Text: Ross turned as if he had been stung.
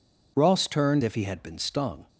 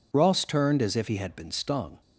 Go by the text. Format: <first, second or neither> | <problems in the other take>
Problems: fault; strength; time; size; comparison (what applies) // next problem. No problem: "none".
second | skips "as"; at 1.0 s